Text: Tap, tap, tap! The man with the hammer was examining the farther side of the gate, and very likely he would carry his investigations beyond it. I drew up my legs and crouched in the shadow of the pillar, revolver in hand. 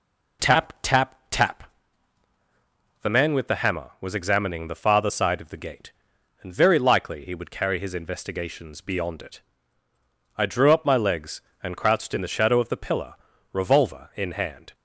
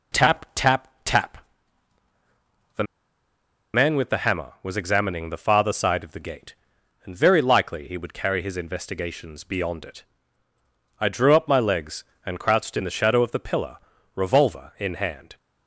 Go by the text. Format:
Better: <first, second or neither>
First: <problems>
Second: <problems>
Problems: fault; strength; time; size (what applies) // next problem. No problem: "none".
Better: first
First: none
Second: pauses between "The" and "man"; noticeable; at 2.8 s; 0.91 s long